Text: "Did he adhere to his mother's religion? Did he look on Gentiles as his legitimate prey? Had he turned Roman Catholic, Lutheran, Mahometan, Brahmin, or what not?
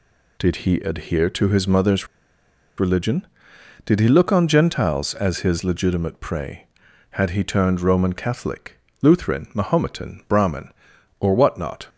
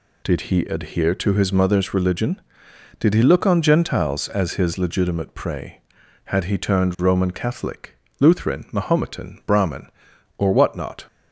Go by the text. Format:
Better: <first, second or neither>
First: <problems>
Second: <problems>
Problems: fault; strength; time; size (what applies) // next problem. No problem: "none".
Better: second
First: pauses between "mother's" and "religion"; noticeable; at 2.0 s; 0.71 s long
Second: none